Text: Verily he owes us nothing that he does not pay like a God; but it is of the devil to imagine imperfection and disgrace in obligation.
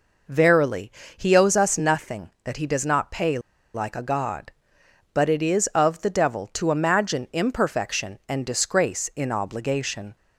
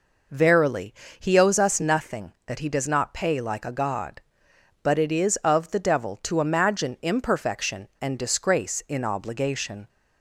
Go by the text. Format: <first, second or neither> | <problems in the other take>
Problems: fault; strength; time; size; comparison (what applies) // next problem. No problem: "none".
second | pauses between "Verily" and "he"; slight; at 0.9 s; 0.26 s long; slight in the second // pauses between "pay" and "like"; slight; at 3.3 s; 0.35 s long